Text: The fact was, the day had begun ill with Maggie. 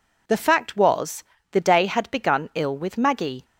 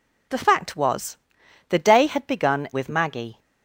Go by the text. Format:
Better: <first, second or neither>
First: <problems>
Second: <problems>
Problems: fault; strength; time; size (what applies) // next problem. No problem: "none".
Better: first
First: none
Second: skips "ill"; at 2.7 s